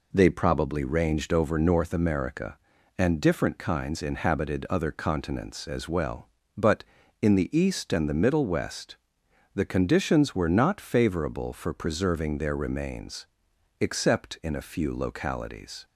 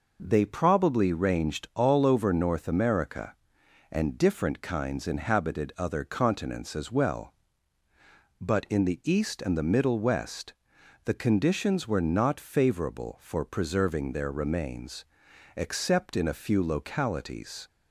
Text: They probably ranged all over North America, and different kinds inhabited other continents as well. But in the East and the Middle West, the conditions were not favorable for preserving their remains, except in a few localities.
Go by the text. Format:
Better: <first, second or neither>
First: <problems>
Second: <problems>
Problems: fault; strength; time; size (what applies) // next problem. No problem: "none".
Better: second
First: skips "all"; at 1.3 s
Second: none